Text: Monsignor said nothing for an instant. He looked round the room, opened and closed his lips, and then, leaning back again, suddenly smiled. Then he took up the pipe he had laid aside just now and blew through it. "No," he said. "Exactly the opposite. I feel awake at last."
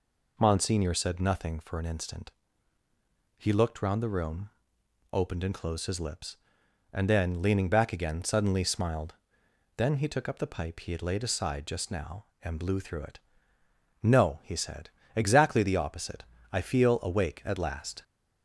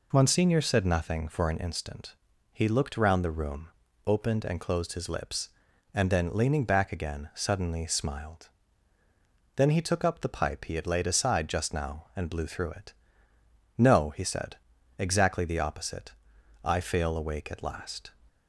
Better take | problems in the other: first | says "fail" for "feel"; at 16.8 s

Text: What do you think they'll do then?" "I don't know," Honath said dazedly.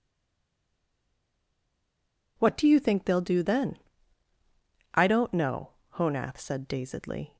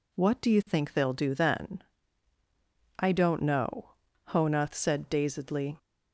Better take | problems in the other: second | stays silent before the first word; until 2.3 s; 2.3 s long

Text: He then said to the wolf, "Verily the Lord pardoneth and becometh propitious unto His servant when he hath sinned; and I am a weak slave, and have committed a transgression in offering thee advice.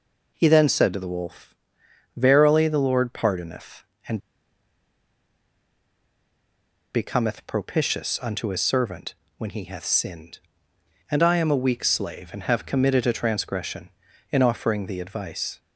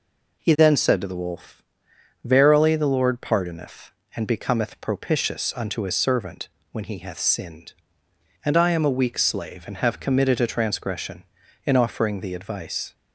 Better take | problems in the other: second | pauses between "and" and "becometh"; strong; at 4.1 s; 2.7 s long // pauses between "servant" and "when"; slight; at 9.1 s; 0.24 s long; slight in the second

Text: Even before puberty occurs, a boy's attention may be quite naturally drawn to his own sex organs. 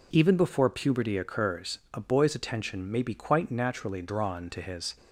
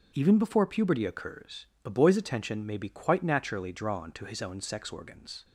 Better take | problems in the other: second | stops before "own sex organs"; at 4.9 s

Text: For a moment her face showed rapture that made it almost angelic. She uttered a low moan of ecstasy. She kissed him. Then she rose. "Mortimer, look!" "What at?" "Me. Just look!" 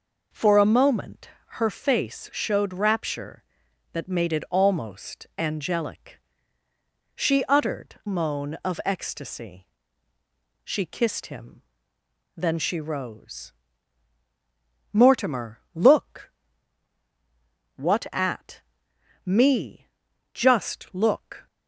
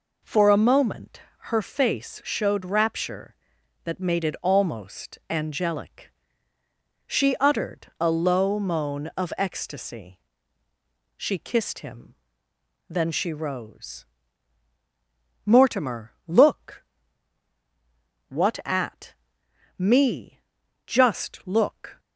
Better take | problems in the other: second | pauses between "moment" and "her"; slight; at 1.2 s; 0.28 s long; slight in the second // skips "a low"; at 8.0 s

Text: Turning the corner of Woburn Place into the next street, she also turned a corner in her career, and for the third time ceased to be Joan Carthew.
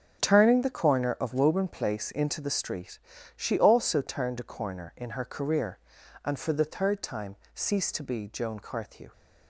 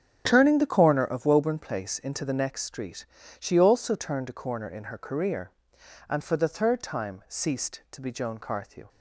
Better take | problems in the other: second | starts louder than the rest; until 1.2 s; 6.5 dB; strong in the second // skips "next"; at 2.4 s // pauses between "time" and "ceased"; slight; at 7.3 s; 0.18 s long

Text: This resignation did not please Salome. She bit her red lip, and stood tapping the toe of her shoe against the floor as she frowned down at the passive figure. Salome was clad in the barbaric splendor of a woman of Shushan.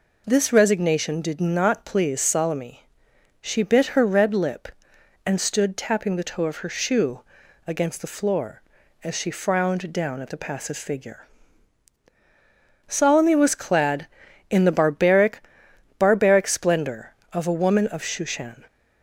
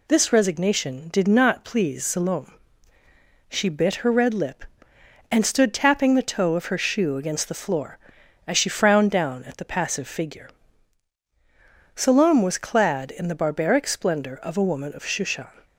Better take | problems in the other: second | pauses between "shoe" and "against"; noticeable; at 7.2 s; 0.46 s long // says "barbaric" twice; at 15.9 s

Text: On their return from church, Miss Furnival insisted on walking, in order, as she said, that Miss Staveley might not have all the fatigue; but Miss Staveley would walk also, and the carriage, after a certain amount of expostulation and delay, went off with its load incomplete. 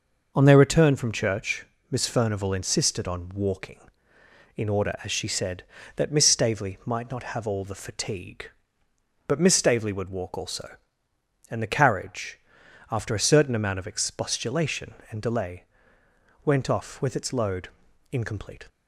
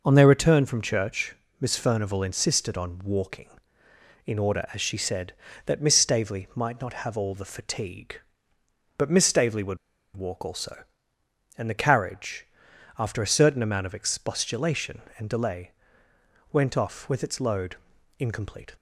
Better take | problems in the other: first | pauses between "would" and "walk"; at 9.7 s; 0.38 s long // pauses between "load" and "incomplete"; at 17.7 s; 0.42 s long; also in the first

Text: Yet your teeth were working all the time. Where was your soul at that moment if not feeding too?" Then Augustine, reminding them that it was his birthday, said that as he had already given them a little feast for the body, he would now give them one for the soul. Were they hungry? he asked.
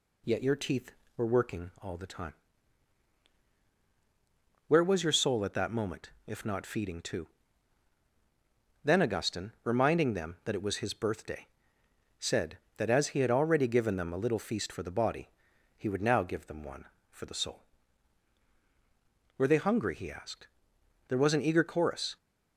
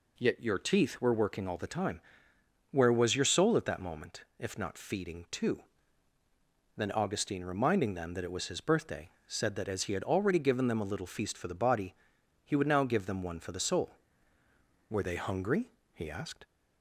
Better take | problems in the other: second | pauses between "moment" and "if"; slight; at 6.0 s; 0.18 s long; slight in the second // goes on to say "There was an eager chorus"; noticeable; from 21.0 s on; 1.0 s long

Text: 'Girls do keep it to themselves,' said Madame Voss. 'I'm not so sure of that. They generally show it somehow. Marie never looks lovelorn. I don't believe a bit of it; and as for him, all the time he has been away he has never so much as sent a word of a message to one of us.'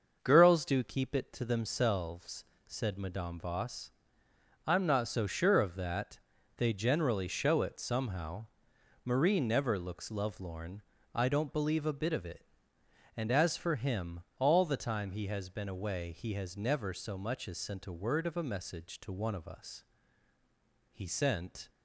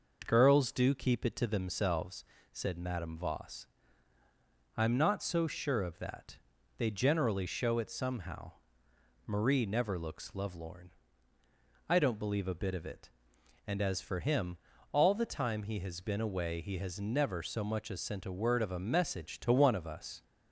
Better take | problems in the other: second | starts louder than the rest; until 1.2 s; 6 dB // goes on to say "He sent"; noticeable; from 20.9 s on; 0.78 s long

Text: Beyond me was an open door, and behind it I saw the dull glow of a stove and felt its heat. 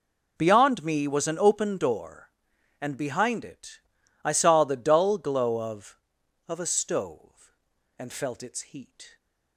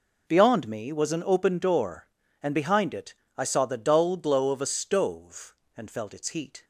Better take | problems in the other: second | pauses between "it" and "I"; at 3.8 s; 0.42 s long; slight in the second // says "of" twice; at 6.4 s

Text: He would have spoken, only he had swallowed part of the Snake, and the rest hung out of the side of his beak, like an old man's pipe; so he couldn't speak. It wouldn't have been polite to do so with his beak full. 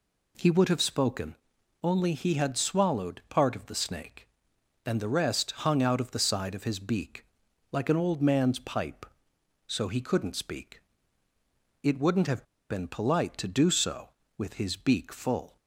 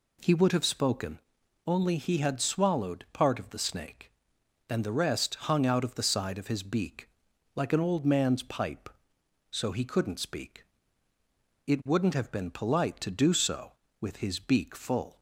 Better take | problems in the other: second | pauses between "have" and "been"; slight; at 12.4 s; 0.25 s long

